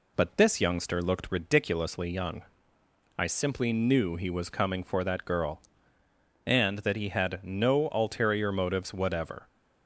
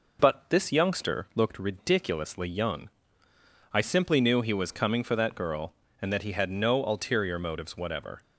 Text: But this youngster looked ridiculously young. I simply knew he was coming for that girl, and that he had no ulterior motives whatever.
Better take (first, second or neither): neither